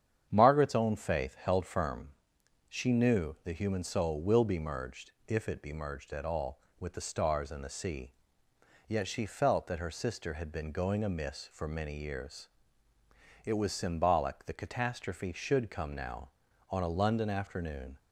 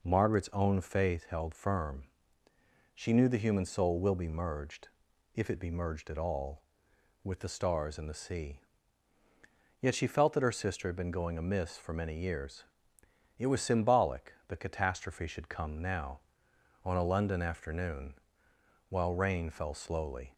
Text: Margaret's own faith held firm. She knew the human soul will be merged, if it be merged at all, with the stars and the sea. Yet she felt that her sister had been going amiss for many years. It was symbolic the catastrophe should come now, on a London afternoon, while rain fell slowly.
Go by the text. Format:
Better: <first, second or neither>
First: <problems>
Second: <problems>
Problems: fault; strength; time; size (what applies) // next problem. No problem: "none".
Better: second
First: starts louder than the rest; strong; until 1.3 s; 8.5 dB // stops before "while rain fell slowly"; at 17.9 s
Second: none